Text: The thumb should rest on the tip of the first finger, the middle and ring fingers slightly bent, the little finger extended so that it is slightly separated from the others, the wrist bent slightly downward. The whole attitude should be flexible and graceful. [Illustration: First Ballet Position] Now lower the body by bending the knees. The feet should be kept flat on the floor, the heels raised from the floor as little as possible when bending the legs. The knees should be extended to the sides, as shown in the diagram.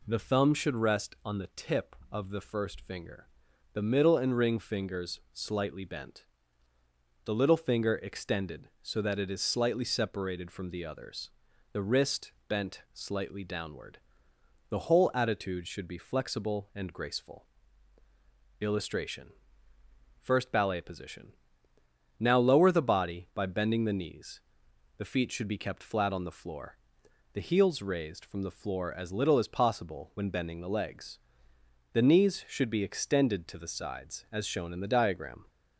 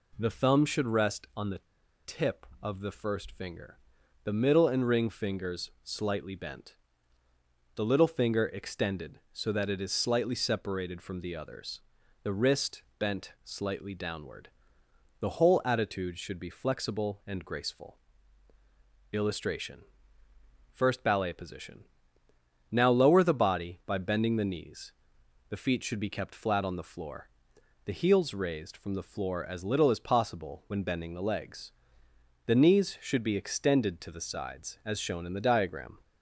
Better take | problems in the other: first | pauses between "the" and "tip"; at 1.5 s; 0.45 s long // pauses between "wrist" and "bent"; slight; at 12.8 s; 0.16 s long; slight in the first // pauses between "Position" and "Now"; noticeable; at 21.8 s; 0.86 s long; noticeable in the first

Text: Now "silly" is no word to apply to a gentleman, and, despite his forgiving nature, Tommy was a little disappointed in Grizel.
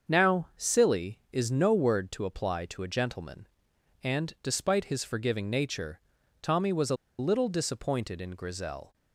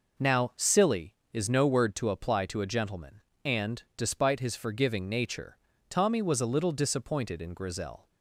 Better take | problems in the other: second | starts louder than the rest; until 1.1 s; 6.5 dB // pauses between "a" and "little"; slight; at 6.9 s; 0.22 s long

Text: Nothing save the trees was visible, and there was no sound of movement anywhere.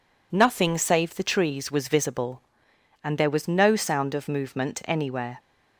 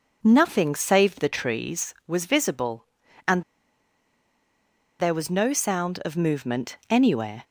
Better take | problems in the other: first | pauses between "and" and "there"; strong; at 3.4 s; 1.5 s long

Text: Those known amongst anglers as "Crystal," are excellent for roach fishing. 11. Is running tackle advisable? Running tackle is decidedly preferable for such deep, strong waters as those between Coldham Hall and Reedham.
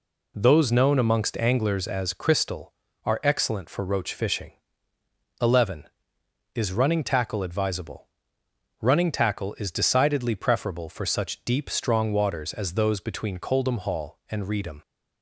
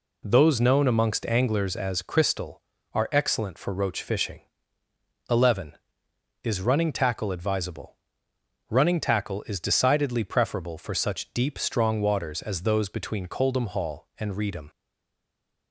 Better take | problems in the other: first | stays silent after the last word; from 14.6 s on; 1.1 s long

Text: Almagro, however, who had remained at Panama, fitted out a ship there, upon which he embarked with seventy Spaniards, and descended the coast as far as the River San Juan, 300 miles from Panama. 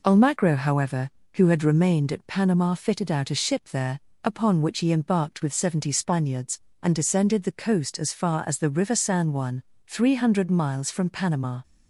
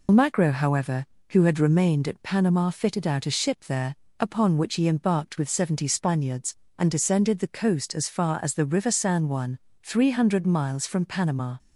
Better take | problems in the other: first | loses the start of "Almagro"; at 0.0 s; 85 ms

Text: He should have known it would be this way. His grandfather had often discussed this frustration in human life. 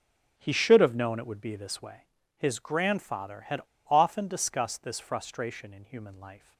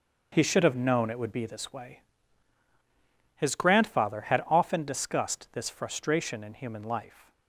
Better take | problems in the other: second | starts louder than the rest; noticeable; until 1.3 s; 6 dB; also in the second // pauses between "had" and "often"; slight; at 3.6 s; 0.26 s long

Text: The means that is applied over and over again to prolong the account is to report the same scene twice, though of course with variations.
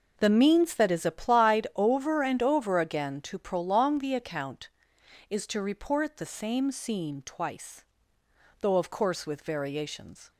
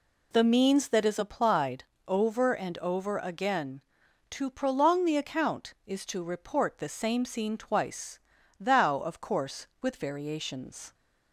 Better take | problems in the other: first | pauses between "applied" and "over"; slight; at 1.8 s; 0.24 s long // says "thou" for "though"; at 8.5 s

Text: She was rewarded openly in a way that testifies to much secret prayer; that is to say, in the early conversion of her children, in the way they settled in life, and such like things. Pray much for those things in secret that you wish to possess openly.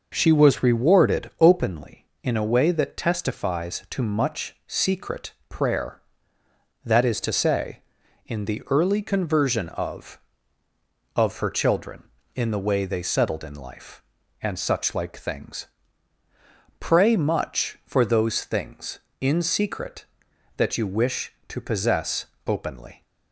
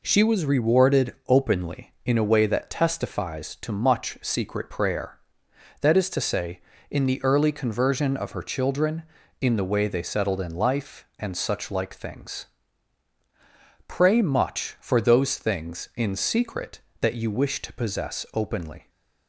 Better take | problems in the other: second | pauses between "secret" and "prayer"; slight; at 5.3 s; 0.16 s long // says "of" twice; at 11.1 s // pauses between "possess" and "openly"; slight; at 22.2 s; 0.18 s long

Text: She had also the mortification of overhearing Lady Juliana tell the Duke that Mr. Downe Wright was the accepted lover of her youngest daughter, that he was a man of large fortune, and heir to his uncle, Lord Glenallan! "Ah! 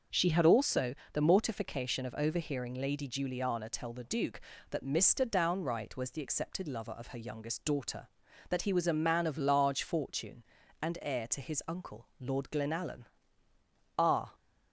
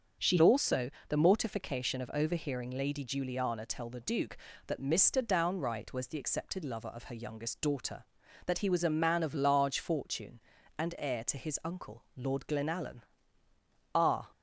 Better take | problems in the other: first | starts louder than the rest; until 1.4 s; 6.5 dB; also in the first // skips "had"; at 0.3 s // pauses between "also" and "the"; slight; at 0.8 s; 0.20 s long; slight in the first

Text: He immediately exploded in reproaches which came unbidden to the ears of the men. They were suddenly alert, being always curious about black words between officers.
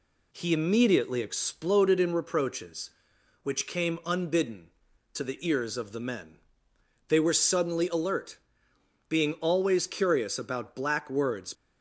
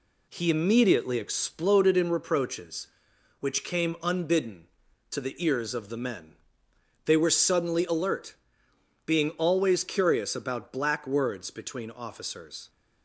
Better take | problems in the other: second | stops before "between officers"; at 11.5 s

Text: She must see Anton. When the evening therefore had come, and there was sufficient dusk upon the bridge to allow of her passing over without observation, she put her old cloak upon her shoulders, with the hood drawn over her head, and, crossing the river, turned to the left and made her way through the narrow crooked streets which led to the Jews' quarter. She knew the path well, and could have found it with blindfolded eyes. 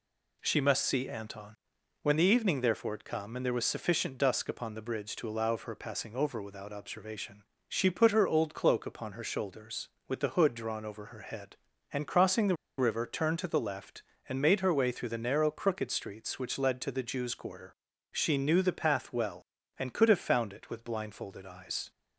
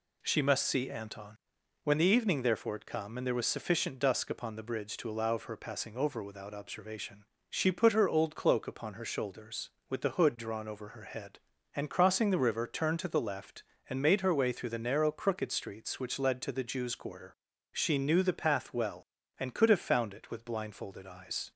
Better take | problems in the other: second | pauses between "the" and "river"; slight; at 12.5 s; 0.22 s long

